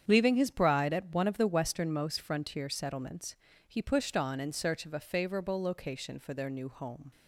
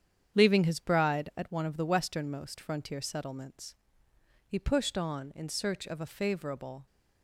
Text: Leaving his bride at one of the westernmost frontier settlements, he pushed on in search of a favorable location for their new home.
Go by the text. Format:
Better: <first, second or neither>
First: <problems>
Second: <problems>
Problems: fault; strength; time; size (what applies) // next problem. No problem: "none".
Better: first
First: starts louder than the rest; strong; until 1.0 s; 8.5 dB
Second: starts louder than the rest; strong; until 1.4 s; 8.5 dB // stops before "location for their new home"; at 6.8 s